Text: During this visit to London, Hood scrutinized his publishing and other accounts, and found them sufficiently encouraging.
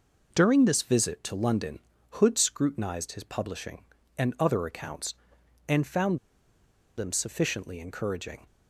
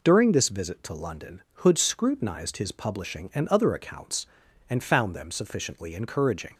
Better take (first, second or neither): second